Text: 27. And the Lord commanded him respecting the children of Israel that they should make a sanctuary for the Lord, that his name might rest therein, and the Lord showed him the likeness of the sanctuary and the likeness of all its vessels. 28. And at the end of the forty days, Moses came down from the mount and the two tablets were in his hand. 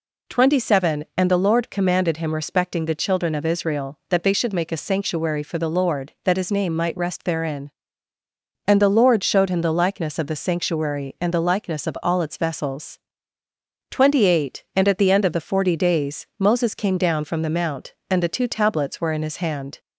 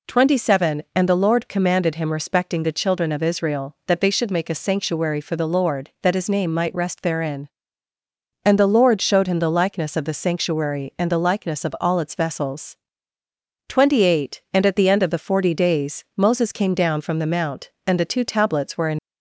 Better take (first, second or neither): first